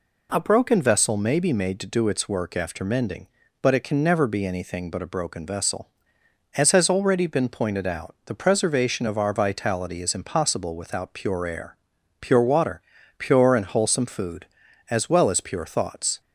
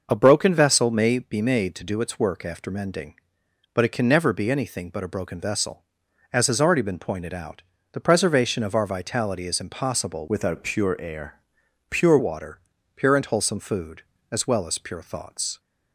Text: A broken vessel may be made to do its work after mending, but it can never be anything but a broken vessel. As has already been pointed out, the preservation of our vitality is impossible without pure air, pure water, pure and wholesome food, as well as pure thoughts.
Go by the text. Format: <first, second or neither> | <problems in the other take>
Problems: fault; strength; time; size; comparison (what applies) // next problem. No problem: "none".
first | changes voice from "without" to "pure"; from 10.2 to 12.1 s; 1.9 s long